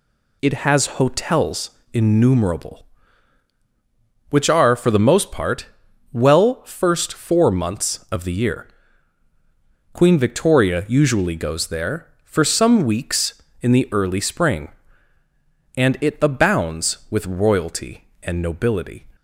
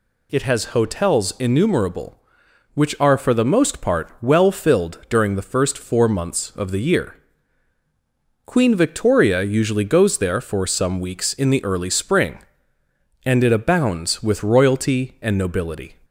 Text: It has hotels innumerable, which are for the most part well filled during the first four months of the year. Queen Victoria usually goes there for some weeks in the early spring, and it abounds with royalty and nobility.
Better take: second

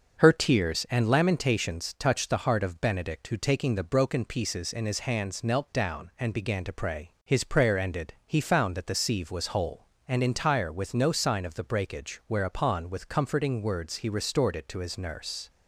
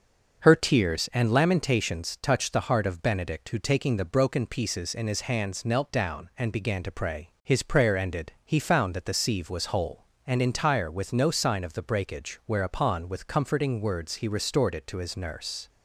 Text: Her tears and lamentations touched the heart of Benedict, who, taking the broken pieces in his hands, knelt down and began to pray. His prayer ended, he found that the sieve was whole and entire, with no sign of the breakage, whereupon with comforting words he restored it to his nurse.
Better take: neither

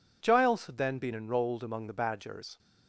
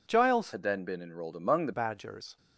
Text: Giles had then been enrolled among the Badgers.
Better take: first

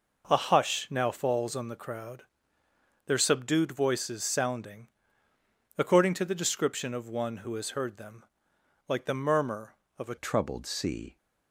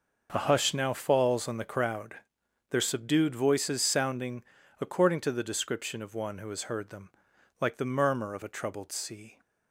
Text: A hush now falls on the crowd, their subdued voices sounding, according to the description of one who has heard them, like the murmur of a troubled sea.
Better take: second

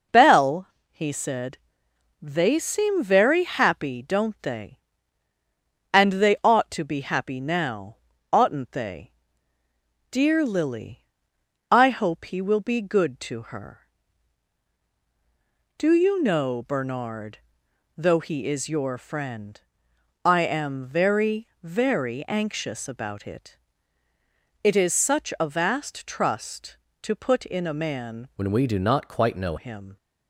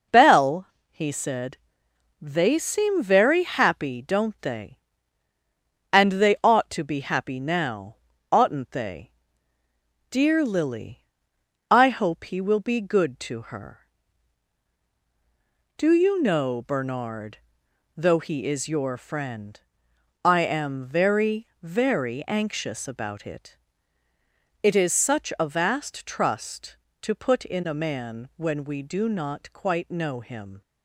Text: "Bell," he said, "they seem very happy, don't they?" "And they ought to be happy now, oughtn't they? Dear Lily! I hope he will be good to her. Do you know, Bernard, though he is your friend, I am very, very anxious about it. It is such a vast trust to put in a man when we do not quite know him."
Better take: second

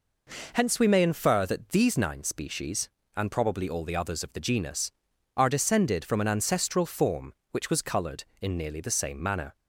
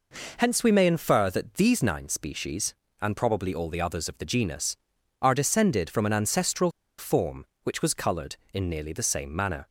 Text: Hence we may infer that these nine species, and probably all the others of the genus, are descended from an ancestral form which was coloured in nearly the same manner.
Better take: first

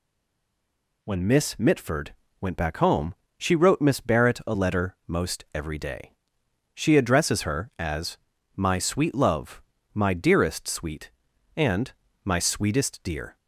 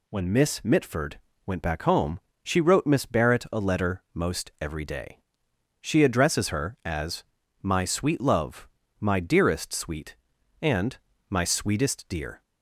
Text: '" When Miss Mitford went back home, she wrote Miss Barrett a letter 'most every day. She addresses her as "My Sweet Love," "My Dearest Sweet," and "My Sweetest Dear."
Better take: second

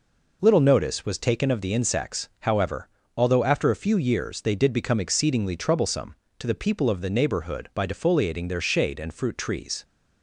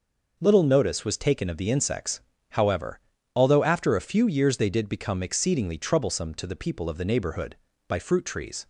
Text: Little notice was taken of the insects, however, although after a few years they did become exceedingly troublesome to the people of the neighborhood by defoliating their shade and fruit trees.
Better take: first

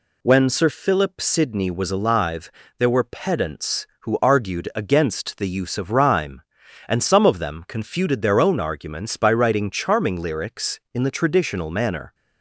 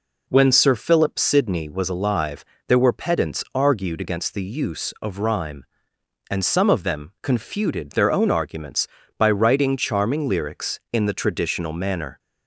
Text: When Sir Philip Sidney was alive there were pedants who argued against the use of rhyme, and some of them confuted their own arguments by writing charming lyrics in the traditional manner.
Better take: first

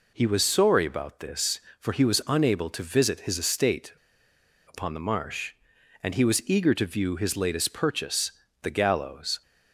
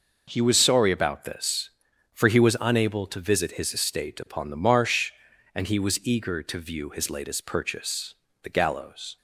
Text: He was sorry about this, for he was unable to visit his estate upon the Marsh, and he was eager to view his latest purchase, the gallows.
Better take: second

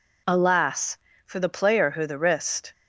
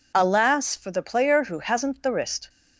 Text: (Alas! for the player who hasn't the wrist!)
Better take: second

